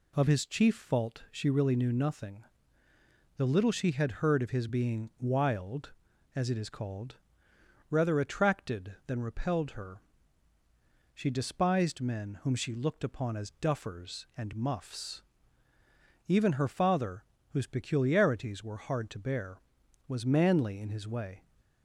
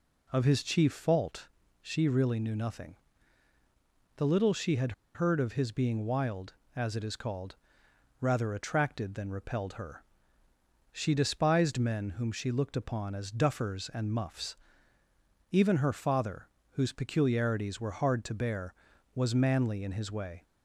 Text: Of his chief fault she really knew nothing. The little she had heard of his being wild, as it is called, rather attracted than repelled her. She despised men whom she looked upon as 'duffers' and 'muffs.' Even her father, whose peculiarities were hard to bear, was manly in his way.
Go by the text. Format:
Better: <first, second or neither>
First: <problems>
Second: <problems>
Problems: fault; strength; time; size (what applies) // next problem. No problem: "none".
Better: first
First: none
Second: pauses between "fault" and "she"; slight; at 1.4 s; 0.34 s long // pauses between "had" and "heard"; slight; at 4.9 s; 0.23 s long